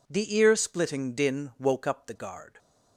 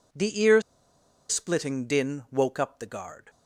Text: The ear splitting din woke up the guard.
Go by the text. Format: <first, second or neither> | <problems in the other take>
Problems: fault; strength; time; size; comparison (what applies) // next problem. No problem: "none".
first | pauses between "ear" and "splitting"; noticeable; at 0.6 s; 0.68 s long